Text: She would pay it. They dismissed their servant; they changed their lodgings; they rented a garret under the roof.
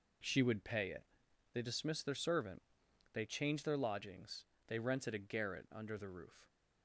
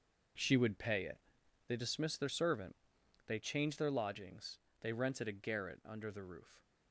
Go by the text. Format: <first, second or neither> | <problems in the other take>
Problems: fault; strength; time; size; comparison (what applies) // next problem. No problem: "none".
first | gets quieter; strong; throughout; 10.5 dB